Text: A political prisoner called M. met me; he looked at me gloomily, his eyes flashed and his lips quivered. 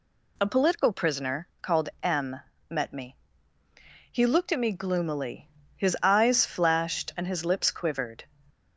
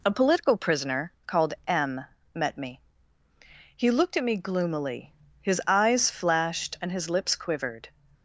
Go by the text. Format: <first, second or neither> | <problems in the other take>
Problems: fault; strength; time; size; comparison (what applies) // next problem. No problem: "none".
first | gets quieter; slight; throughout; 2.5 dB // pauses between "prisoner" and "called"; slight; at 1.1 s; 0.16 s long; slight in the first